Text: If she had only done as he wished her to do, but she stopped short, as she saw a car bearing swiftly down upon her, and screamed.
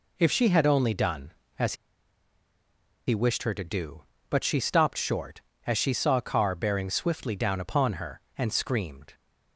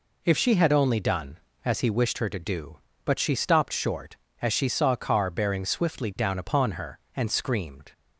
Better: second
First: pauses between "as" and "he"; strong; at 1.7 s; 1.3 s long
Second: none

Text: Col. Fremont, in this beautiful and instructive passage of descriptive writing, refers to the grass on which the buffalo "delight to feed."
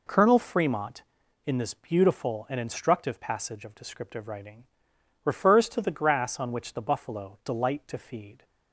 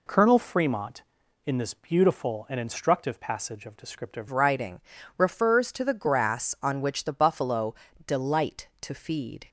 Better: first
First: none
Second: changes voice at "writing"; from 4.3 s on; 5.1 s long // pauses between "buffalo" and "delight"; slight; at 7.7 s; 0.32 s long

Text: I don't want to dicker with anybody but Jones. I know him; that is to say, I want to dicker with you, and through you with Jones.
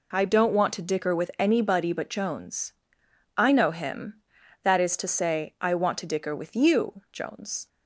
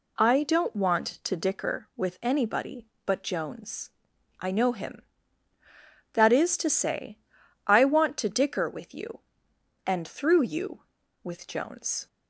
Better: second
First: skips "and through you with"; at 7.0 s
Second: none

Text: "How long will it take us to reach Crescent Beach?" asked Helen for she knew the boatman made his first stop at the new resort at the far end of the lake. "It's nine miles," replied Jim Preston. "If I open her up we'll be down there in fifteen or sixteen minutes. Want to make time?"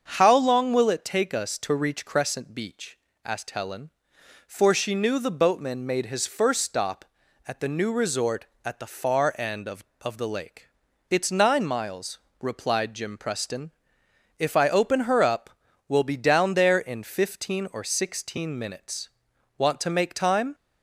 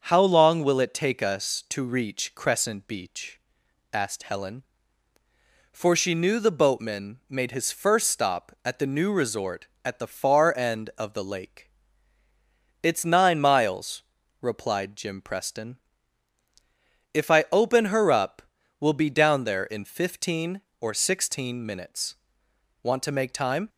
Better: second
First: starts louder than the rest; until 1.1 s; 7 dB // says "of" twice; at 10.0 s // pauses between "up" and "we'll"; at 15.5 s; 0.38 s long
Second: starts louder than the rest; until 1.0 s; 6.5 dB // pauses between "up" and "we'll"; at 18.4 s; 0.38 s long

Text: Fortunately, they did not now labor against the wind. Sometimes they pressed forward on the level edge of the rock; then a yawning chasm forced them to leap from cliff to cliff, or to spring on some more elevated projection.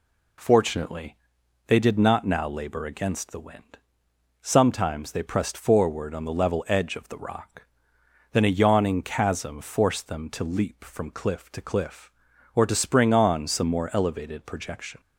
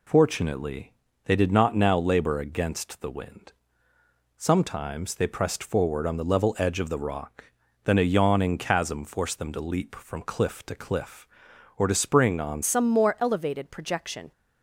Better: first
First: none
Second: changes voice at "some"; from 12.6 s on; 1.7 s long

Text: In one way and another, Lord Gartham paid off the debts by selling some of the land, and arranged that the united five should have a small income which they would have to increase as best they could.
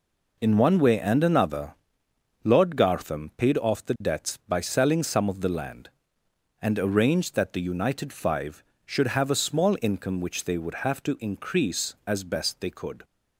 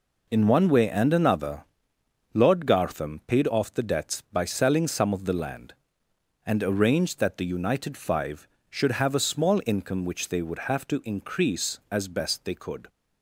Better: neither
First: none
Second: none

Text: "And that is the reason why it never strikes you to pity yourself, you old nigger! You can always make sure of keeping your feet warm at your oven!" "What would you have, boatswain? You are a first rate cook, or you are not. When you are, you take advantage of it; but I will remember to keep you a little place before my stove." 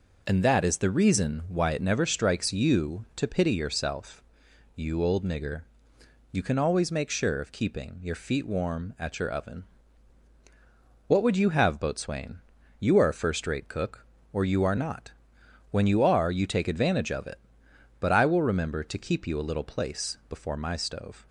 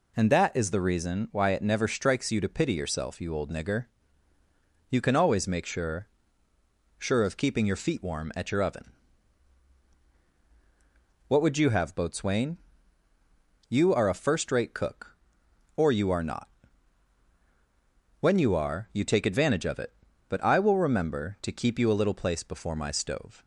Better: first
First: none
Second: says "sure" twice; at 6.9 s

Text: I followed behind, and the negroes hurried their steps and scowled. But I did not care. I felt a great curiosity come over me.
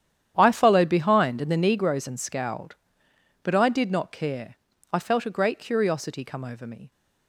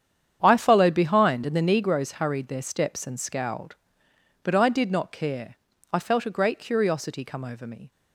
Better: second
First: starts louder than the rest; strong; until 1.3 s; 10 dB // skips "hurried their steps"; at 2.0 s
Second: starts louder than the rest; strong; until 1.4 s; 8.5 dB

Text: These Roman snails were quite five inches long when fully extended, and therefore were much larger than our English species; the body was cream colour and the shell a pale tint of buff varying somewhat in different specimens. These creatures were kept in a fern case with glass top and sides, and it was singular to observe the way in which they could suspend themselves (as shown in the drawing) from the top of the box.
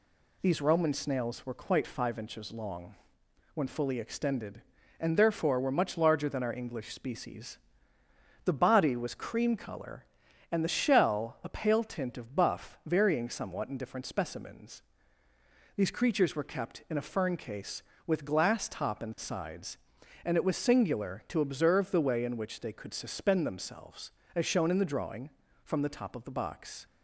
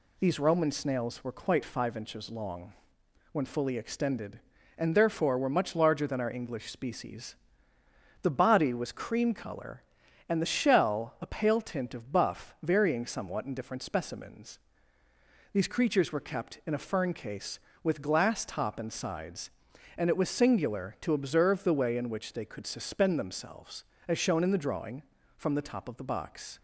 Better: neither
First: pauses between "long" and "when"; noticeable; at 2.9 s; 0.60 s long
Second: pauses between "long" and "when"; noticeable; at 2.7 s; 0.60 s long

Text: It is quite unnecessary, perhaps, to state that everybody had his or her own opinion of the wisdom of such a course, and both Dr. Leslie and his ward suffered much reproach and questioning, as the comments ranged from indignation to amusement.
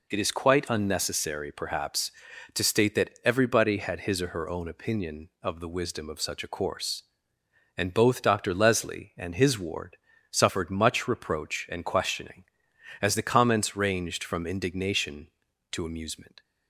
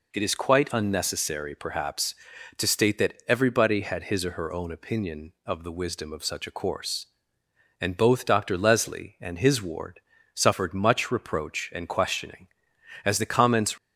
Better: first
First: pauses between "ward" and "suffered"; slight; at 9.9 s; 0.34 s long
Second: pauses between "ward" and "suffered"; slight; at 9.9 s; 0.34 s long // stops before "ranged from indignation to amusement"; at 13.7 s

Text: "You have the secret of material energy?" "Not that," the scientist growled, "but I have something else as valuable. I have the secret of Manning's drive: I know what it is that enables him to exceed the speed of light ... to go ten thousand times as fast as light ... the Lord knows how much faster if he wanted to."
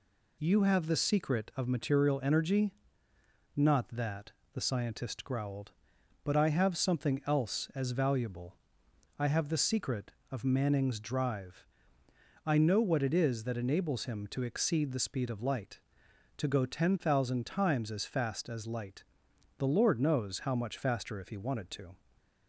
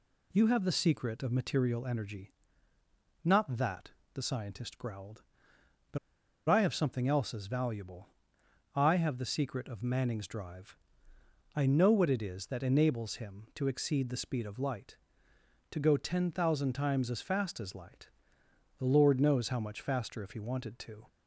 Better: first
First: none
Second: pauses between "but" and "I"; noticeable; at 5.9 s; 0.51 s long

